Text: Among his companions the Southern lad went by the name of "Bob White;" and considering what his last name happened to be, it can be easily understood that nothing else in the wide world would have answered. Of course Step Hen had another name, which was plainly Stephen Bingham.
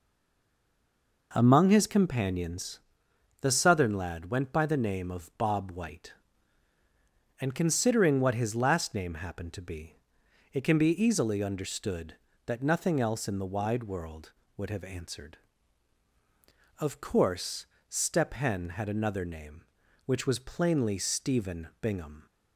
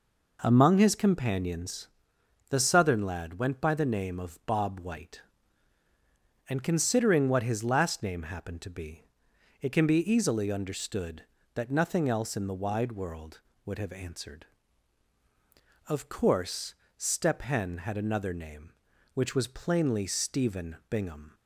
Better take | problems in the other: second | stays silent before the first word; noticeable; until 1.3 s; 1.3 s long // pauses between "companions" and "the"; noticeable; at 2.7 s; 0.60 s long; noticeable in the second // pauses between "course" and "Step"; slight; at 17.6 s; 0.24 s long; slight in the second

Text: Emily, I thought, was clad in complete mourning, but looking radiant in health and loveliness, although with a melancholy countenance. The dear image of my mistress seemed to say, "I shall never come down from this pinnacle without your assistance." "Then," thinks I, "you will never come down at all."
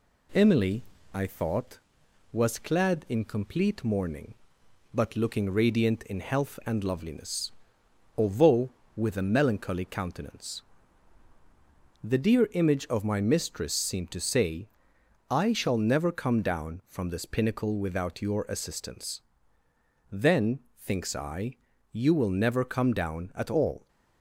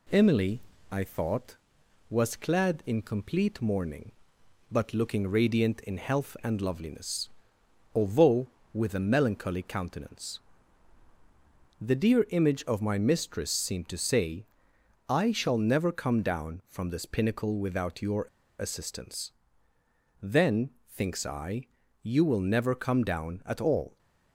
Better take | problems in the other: first | pauses between "your" and "assistance"; at 18.2 s; 0.36 s long

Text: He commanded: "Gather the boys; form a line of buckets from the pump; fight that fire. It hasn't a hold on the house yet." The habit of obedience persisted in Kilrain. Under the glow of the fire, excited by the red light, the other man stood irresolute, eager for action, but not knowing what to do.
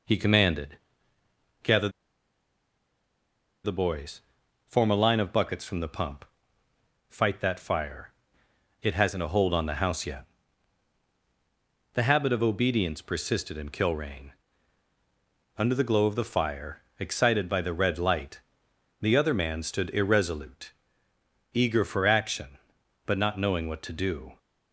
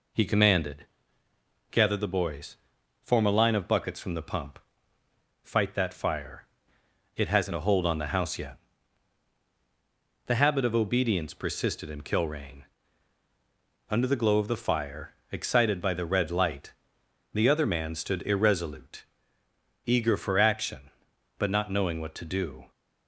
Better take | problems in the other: second | pauses between "Gather" and "the"; strong; at 1.8 s; 1.7 s long

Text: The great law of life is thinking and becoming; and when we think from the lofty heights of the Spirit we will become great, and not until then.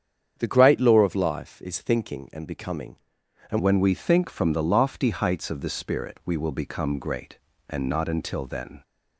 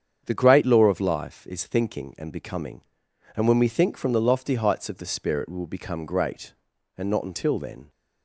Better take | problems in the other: second | starts louder than the rest; strong; until 1.3 s; 8.5 dB; strong in the second // changes voice at "when"; from 3.5 s on; 5.3 s long

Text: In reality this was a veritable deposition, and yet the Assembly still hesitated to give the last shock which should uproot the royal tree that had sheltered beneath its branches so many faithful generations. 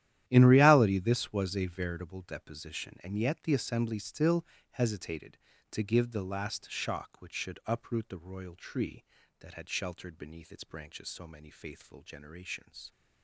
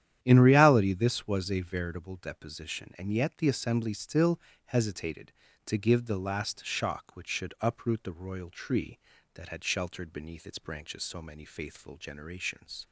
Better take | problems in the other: second | gets quieter; strong; throughout; 15 dB // starts louder than the rest; strong; until 1.2 s; 12 dB; strong in the second // pauses between "still" and "hesitated"; slight; at 4.4 s; 0.28 s long; slight in the second

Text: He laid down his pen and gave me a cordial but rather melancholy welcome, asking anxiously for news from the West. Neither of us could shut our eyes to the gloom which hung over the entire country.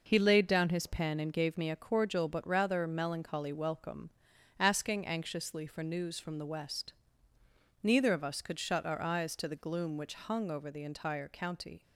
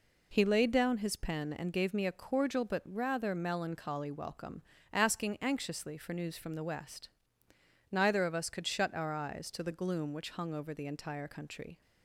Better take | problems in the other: second | says "county" for "country"; at 11.2 s

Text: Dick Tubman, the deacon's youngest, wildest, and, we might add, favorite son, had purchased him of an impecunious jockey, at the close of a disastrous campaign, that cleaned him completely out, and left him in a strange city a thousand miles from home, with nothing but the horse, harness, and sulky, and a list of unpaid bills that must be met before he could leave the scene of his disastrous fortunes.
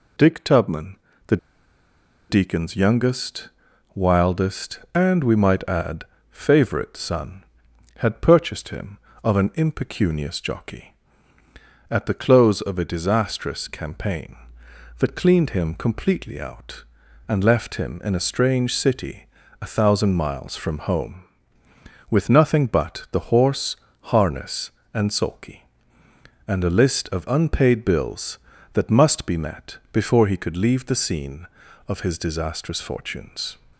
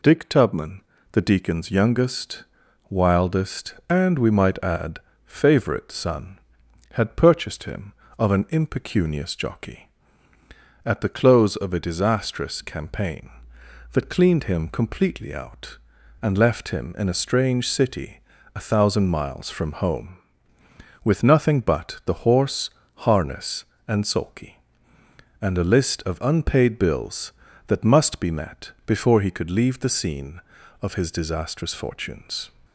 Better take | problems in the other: second | pauses between "the" and "deacon's"; noticeable; at 1.3 s; 0.93 s long // pauses between "city" and "a"; slight; at 19.2 s; 0.34 s long; slight in the second

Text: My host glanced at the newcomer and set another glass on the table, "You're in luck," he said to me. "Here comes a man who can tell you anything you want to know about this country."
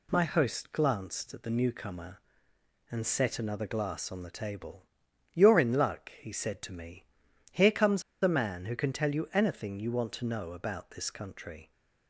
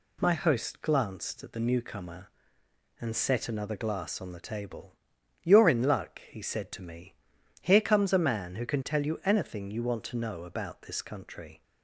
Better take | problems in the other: second | pauses between "comes" and "a"; slight; at 8.0 s; 0.20 s long

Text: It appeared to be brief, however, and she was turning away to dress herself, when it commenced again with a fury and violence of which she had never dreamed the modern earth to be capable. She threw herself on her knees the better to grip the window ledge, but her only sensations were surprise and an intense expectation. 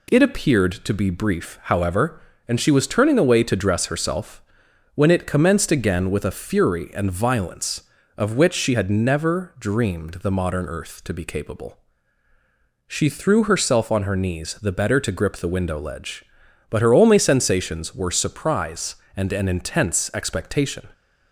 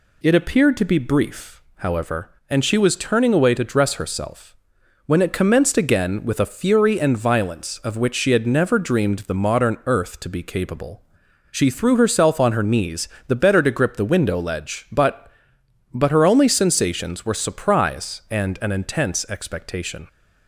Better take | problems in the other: first | pauses between "knees" and "the"; slight; at 13.0 s; 0.20 s long // says "but" twice; at 15.9 s

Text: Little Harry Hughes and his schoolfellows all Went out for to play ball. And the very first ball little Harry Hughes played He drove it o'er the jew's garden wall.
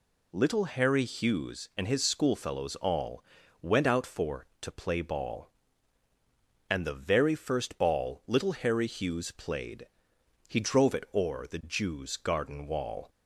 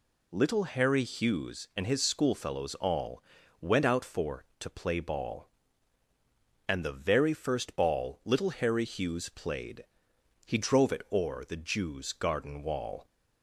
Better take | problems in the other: neither | pauses between "all" and "Went"; the same in both // pauses between "played" and "He"; noticeable; the same in both

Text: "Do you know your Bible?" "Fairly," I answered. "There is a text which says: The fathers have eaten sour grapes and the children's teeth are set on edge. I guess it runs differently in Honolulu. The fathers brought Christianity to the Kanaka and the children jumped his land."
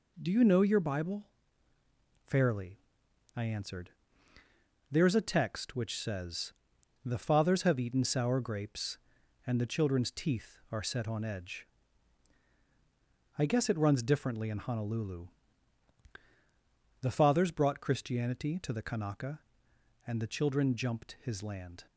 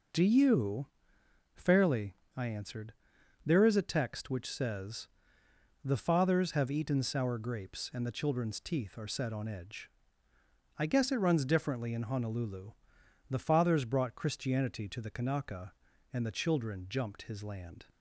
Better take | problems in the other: first | skips "know your Bible"; at 1.2 s

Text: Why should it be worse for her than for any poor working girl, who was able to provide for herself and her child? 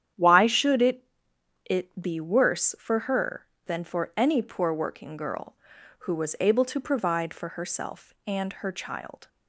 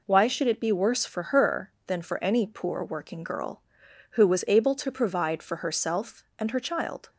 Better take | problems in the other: second | starts louder than the rest; strong; until 1.7 s; 9.5 dB // says "it" twice; at 1.6 s

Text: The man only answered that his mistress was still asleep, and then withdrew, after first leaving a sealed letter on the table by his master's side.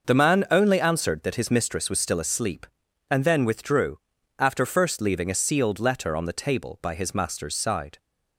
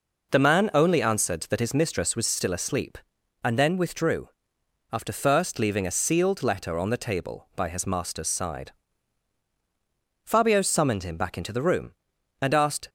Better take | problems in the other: first | goes on to say "Fabio summoned him back into the room and asked"; strong; from 10.2 s on; 2.6 s long

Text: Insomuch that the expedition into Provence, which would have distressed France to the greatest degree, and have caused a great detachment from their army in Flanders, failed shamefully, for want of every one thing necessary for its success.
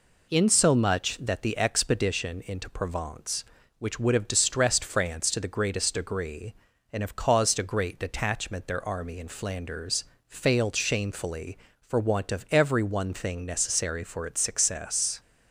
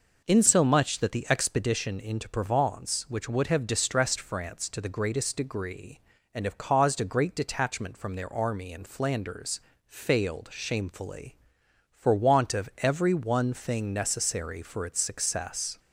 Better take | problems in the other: second | skips "from"; at 8.6 s

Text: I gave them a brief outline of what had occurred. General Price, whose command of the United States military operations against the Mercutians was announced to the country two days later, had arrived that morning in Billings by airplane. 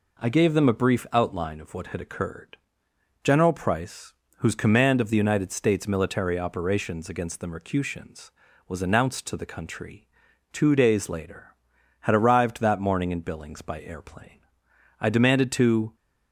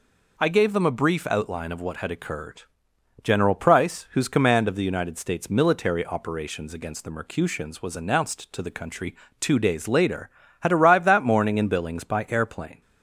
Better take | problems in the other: second | pauses between "country" and "two"; at 10.0 s; 0.44 s long; slight in the second // goes on to say "I demanded to"; noticeable; from 14.9 s on; 0.96 s long

